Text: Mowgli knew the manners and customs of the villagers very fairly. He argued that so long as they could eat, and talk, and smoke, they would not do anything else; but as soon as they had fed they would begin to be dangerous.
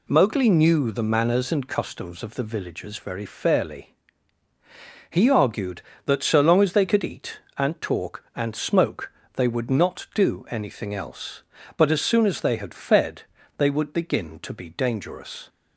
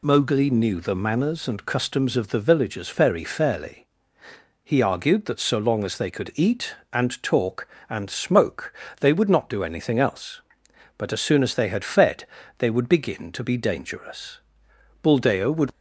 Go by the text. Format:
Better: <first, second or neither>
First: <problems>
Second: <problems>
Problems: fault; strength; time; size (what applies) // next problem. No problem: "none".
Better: first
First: pauses between "fed" and "they"; slight; at 13.2 s; 0.34 s long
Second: pauses between "fed" and "they"; slight; at 12.2 s; 0.32 s long // goes on to say "Buldeo would"; noticeable; from 15.0 s on; 0.68 s long